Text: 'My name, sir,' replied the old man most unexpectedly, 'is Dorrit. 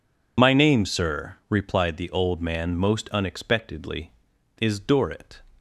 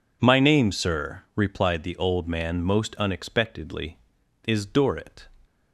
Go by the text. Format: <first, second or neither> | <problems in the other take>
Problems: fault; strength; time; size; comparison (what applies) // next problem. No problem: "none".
second | loses the start of "My"; at 0.3 s; 25 ms